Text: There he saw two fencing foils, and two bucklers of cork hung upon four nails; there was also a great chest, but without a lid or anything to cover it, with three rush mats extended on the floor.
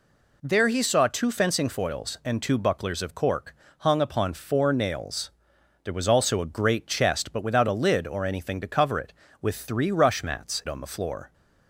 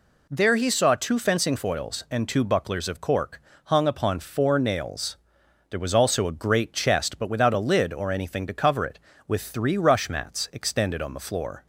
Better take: second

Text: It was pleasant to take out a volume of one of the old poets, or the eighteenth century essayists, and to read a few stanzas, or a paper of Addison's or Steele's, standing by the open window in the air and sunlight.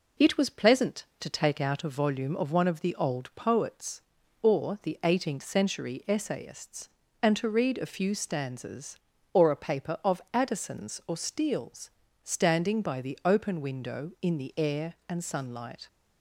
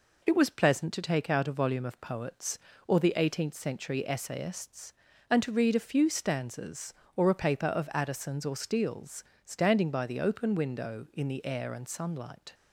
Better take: first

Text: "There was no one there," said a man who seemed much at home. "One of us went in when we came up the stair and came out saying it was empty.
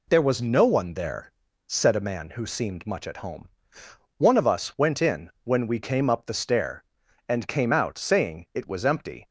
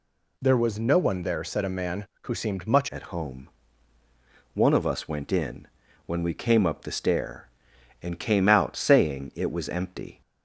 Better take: first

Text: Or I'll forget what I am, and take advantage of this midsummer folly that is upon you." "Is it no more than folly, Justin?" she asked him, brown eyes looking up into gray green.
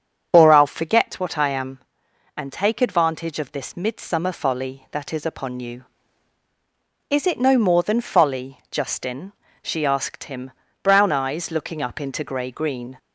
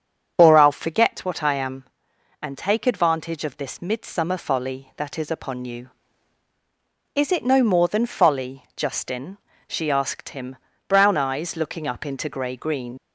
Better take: first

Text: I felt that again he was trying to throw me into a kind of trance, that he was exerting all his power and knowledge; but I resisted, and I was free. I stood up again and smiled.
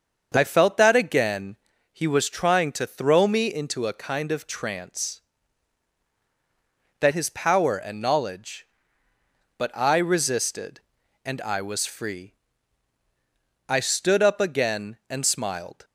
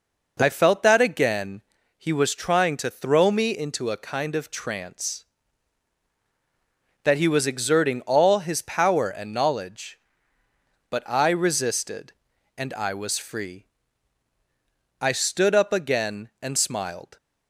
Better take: second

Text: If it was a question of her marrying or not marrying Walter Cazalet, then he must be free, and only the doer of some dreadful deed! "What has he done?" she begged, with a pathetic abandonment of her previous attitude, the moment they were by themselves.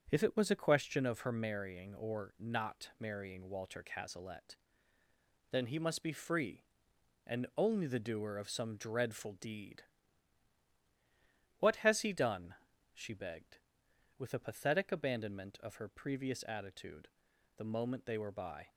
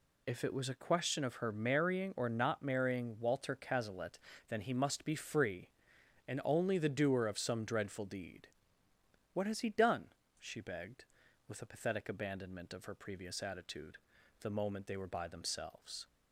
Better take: second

